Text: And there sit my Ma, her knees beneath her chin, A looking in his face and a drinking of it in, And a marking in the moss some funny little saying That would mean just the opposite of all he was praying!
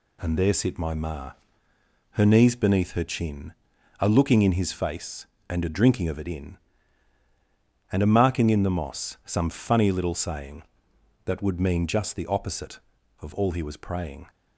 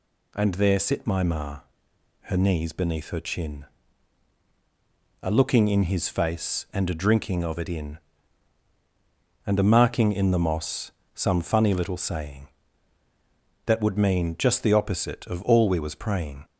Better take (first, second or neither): first